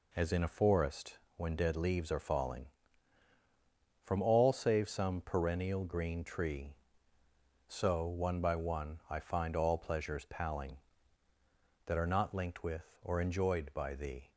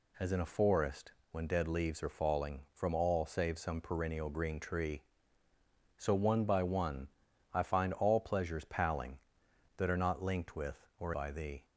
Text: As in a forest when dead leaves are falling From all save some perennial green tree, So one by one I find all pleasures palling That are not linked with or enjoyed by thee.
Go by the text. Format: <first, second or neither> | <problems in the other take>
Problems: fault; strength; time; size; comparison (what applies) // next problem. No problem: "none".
first | pauses between "forest" and "when"; slight; at 1.1 s; 0.20 s long; slight in the first // pauses between "one" and "I"; at 7.0 s; 0.42 s long // skips "enjoyed"; at 11.1 s